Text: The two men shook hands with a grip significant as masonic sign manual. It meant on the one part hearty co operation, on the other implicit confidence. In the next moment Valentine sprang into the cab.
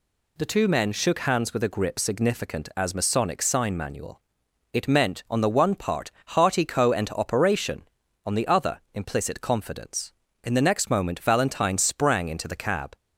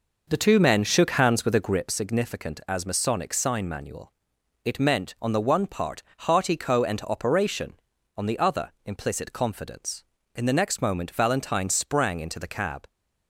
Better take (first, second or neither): first